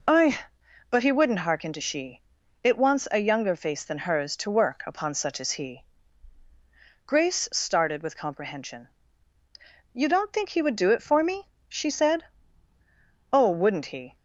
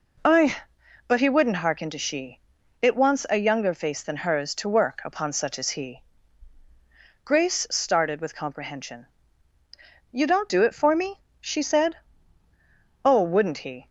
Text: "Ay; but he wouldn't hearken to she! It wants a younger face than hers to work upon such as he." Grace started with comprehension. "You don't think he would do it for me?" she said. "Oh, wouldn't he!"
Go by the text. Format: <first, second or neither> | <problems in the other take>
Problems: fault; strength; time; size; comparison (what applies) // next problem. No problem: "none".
first | skips "think he would"; at 10.4 s